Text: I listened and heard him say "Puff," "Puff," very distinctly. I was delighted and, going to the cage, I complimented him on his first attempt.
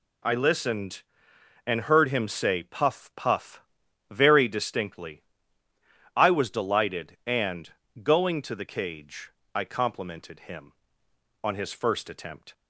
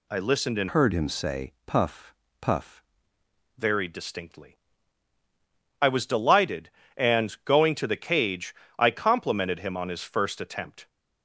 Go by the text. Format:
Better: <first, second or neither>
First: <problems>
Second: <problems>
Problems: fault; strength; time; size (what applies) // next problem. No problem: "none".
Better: first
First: none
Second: changes voice from "heard" to "Puff"; from 0.6 to 2.8 s; 2.2 s long